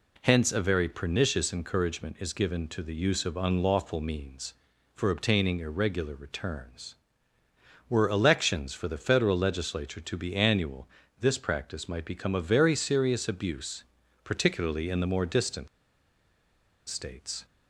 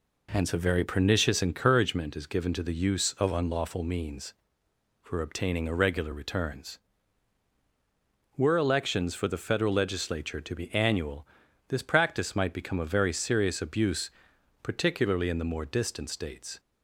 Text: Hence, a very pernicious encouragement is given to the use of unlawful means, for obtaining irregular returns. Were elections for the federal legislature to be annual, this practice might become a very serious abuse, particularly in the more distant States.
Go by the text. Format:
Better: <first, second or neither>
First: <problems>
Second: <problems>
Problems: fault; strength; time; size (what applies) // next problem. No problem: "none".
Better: second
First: pauses between "distant" and "States"; at 15.6 s; 1.2 s long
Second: none